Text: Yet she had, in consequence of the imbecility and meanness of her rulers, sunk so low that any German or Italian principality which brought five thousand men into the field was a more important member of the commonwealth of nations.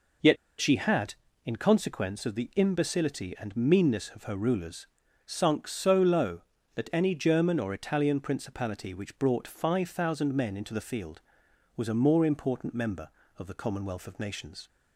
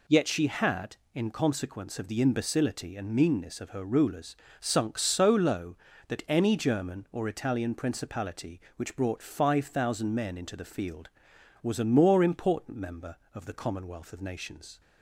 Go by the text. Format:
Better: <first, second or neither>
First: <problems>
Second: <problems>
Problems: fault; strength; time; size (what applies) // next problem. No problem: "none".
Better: second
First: pauses between "Yet" and "she"; slight; at 0.3 s; 0.22 s long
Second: none